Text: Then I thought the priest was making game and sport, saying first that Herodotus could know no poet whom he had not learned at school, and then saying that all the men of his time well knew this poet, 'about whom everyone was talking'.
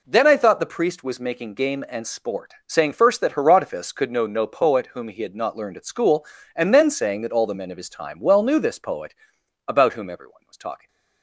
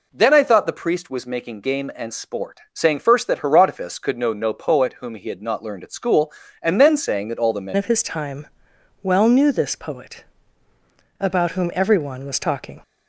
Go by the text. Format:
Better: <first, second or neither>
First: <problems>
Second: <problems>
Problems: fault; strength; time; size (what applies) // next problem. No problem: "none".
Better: first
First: none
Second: changes voice at "of"; from 7.7 s on; 5.1 s long // pauses between "time" and "well"; noticeable; at 8.4 s; 0.56 s long